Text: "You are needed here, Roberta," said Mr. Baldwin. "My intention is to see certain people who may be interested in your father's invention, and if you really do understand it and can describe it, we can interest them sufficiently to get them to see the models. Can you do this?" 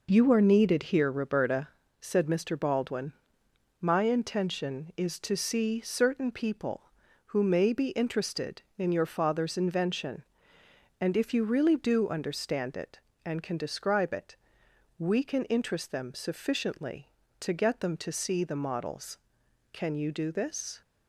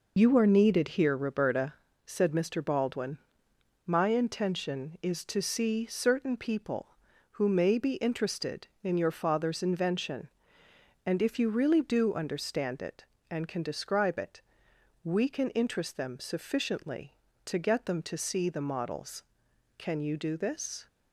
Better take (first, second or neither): first